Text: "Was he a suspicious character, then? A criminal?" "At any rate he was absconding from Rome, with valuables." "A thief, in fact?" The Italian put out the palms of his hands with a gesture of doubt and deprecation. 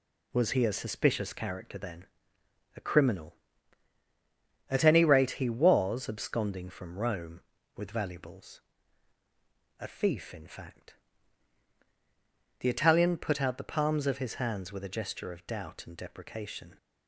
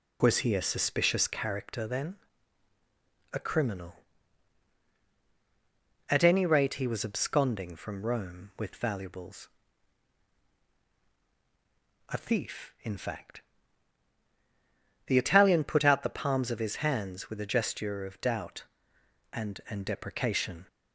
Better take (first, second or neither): first